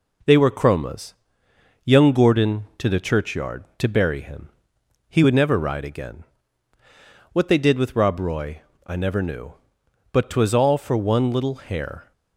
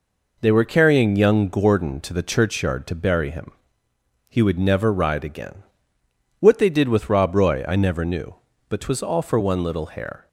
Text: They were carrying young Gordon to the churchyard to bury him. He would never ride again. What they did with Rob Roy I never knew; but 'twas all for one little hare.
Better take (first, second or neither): second